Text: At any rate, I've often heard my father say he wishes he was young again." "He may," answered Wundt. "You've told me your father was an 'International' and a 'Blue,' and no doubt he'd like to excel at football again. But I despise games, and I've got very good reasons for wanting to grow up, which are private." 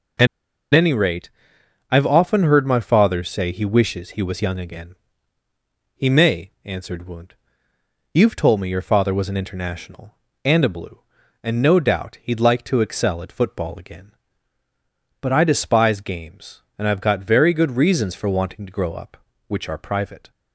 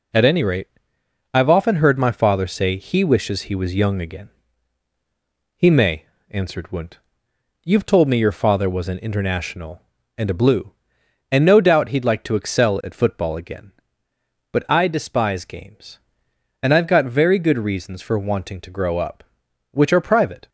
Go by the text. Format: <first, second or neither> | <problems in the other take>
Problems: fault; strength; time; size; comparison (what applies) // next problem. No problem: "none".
second | pauses between "At" and "any"; noticeable; at 0.2 s; 0.47 s long